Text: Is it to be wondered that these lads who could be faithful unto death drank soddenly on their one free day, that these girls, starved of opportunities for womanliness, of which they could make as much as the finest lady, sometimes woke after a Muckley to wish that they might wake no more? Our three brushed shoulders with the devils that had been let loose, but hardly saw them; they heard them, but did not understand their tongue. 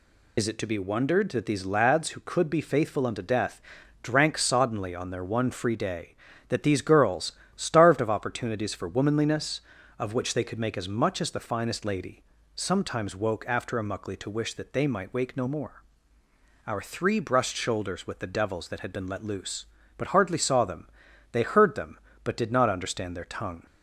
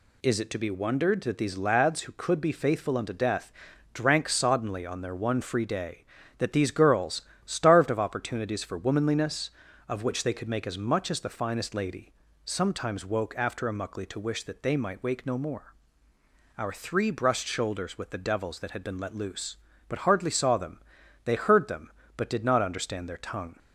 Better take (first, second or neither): second